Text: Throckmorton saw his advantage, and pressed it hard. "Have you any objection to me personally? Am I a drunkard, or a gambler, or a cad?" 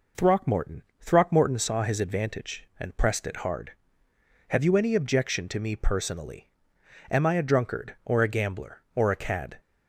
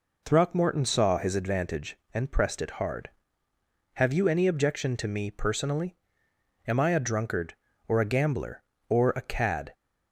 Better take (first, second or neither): second